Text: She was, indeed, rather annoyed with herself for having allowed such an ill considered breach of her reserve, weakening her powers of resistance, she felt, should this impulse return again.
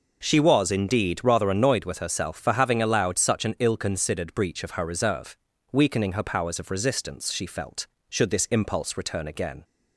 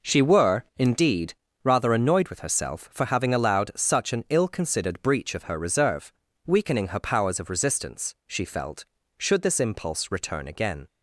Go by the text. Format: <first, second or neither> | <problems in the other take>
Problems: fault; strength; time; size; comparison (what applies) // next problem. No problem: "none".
first | says "were" for "was"; at 0.2 s